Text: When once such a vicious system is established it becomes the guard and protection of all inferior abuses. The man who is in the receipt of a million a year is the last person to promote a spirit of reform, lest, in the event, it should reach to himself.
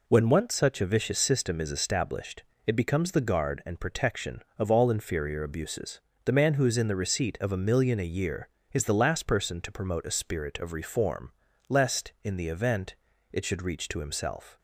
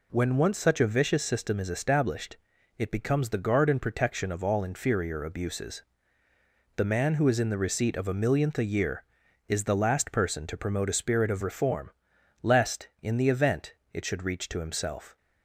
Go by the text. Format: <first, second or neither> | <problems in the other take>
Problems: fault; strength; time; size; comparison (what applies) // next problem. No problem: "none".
first | pauses between "established" and "it"; at 2.3 s; 0.42 s long; slight in the first // says "millionth" for "million"; at 8.1 s